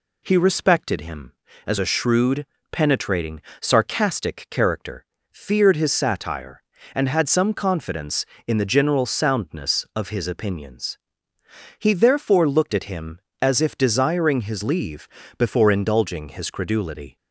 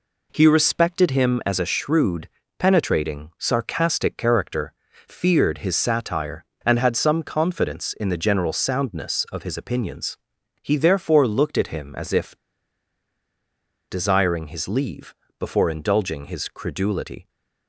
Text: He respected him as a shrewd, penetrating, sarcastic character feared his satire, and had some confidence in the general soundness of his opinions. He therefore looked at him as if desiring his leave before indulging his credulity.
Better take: first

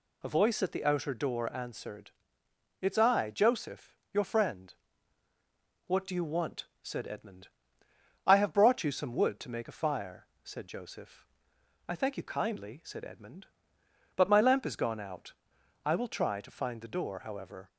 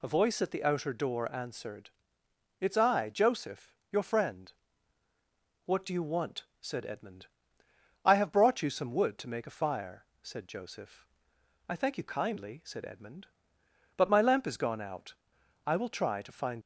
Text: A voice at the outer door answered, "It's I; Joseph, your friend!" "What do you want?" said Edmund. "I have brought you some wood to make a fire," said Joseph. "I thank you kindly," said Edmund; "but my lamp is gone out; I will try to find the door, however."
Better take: first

